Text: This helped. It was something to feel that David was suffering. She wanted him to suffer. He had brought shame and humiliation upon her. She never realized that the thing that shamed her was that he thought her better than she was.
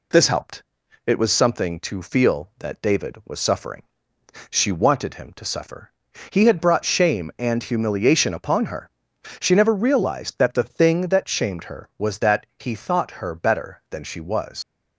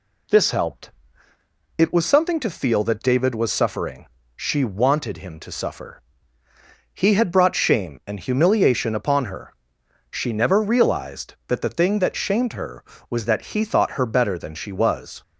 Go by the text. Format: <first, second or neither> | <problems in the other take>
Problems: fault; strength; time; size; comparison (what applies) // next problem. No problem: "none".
second | leaves "was" unfinished; at 14.6 s; 75 ms